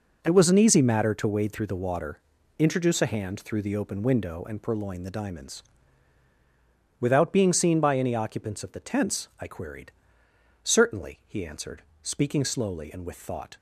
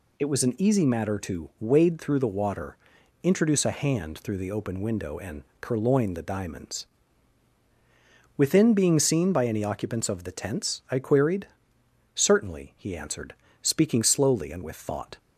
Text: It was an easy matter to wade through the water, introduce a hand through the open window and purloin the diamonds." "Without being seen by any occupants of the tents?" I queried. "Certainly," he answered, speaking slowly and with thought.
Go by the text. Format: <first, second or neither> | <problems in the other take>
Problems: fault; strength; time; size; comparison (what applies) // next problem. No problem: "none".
first | pauses between "and" and "purloin"; slight; at 5.4 s; 0.16 s long // says "Within" for "Without"; at 8.3 s